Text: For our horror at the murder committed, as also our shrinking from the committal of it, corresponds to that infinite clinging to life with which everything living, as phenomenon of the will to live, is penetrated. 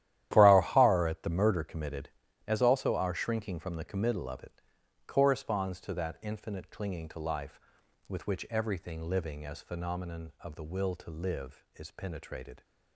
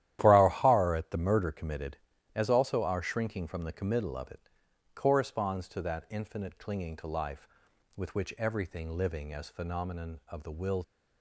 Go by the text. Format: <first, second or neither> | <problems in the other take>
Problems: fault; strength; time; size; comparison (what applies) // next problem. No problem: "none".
first | starts louder than the rest; strong; until 1.2 s; 12.5 dB; strong in the first // stops before "to live is penetrated"; at 10.8 s